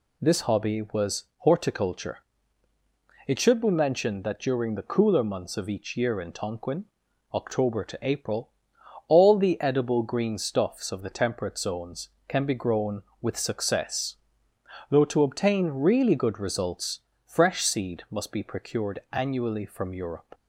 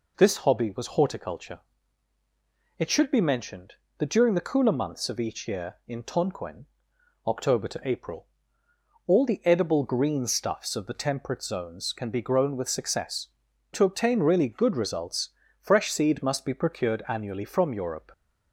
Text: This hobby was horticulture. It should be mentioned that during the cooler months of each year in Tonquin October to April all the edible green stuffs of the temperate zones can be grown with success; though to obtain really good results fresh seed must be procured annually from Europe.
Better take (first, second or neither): first